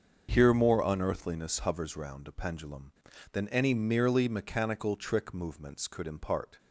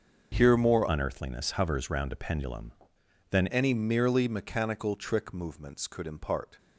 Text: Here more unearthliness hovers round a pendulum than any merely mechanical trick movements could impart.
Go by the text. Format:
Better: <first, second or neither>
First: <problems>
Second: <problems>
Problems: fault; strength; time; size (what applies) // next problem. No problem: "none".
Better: first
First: starts louder than the rest; until 1.3 s; 6.5 dB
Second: starts louder than the rest; until 1.3 s; 6 dB // changes voice from "unearthliness" to "than"; from 0.8 to 3.4 s; 2.6 s long